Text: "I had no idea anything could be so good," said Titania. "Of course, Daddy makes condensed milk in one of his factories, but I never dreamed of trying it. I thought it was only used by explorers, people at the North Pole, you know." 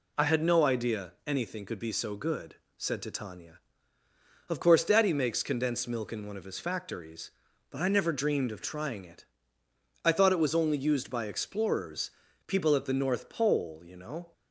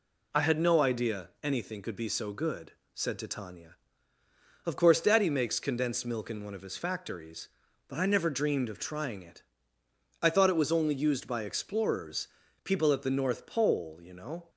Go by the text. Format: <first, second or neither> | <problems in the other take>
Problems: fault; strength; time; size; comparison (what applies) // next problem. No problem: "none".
neither | none